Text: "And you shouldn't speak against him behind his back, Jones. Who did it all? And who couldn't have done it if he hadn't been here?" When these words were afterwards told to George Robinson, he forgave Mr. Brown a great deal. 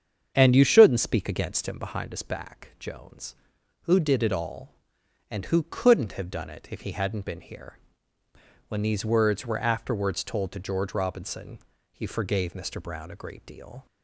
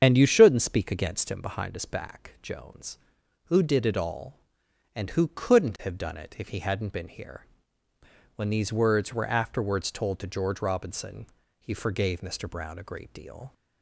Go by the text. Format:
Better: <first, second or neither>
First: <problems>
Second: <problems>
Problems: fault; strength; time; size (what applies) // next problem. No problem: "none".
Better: first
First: starts louder than the rest; strong; until 1.3 s; 7.5 dB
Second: loses the start of "And"; at 0.0 s; 55 ms // starts louder than the rest; strong; until 1.0 s; 7.5 dB